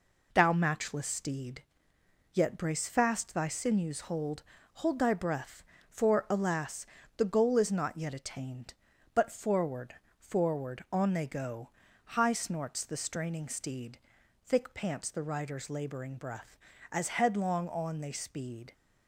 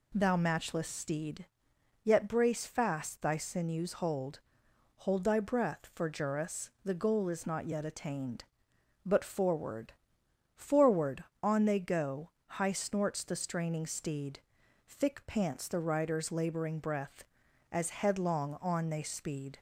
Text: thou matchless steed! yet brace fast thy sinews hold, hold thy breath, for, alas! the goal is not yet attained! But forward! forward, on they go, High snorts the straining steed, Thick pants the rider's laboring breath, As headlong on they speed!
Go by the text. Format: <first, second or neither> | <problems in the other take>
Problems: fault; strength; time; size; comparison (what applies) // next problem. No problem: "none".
first | says "juris" for "alas"; at 6.0 s